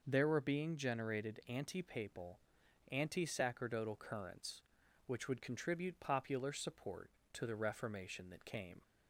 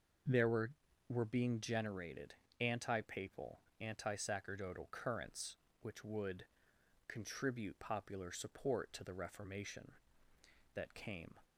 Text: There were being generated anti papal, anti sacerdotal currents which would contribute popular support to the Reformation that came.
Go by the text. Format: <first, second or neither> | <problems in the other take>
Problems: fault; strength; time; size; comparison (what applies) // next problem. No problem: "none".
first | says "were" twice; at 1.0 s // pauses between "generated" and "anti"; slight; at 2.3 s; 0.26 s long // pauses between "would" and "contribute"; noticeable; at 6.4 s; 0.63 s long